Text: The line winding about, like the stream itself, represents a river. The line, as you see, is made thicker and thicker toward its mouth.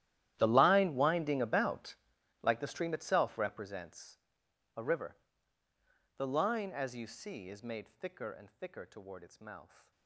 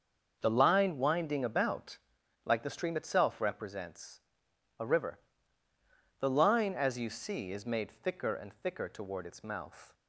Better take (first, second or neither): second